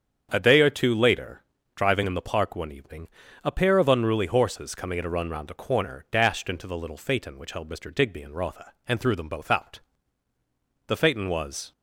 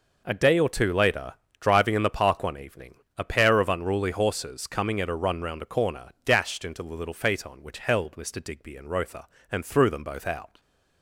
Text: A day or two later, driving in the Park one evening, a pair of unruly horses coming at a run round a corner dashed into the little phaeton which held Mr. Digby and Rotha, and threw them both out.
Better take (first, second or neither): second